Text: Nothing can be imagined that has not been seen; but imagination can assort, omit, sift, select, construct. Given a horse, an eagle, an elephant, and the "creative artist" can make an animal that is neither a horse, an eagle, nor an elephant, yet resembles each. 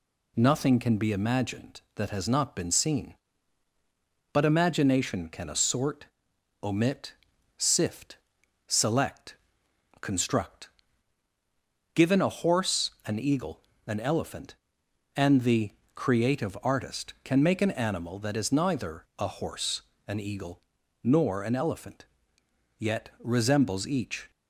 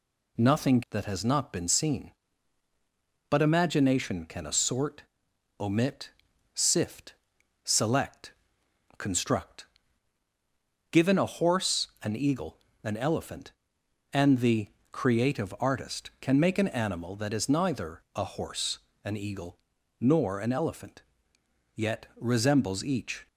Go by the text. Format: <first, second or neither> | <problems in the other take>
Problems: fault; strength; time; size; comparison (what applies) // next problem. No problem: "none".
first | skips "can be imagined"; at 0.8 s // pauses between "the" and "creative"; slight; at 14.6 s; 0.22 s long; slight in the first